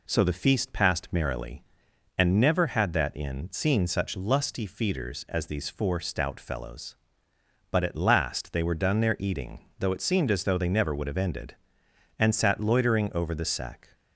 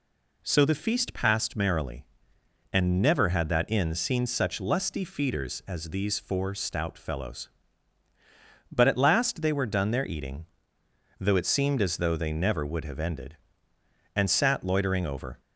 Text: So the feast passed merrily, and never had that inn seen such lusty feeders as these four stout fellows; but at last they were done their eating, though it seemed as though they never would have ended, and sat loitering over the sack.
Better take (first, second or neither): first